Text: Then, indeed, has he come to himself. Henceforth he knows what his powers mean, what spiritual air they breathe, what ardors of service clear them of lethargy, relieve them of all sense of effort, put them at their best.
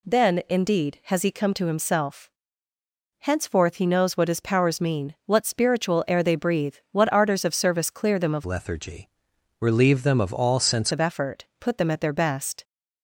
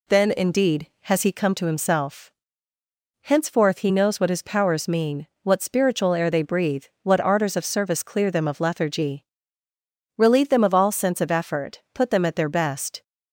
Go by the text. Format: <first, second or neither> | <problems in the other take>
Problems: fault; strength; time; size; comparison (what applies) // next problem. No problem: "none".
second | changes voice from "lethargy" to "sense"; from 8.4 to 10.9 s; 2.5 s long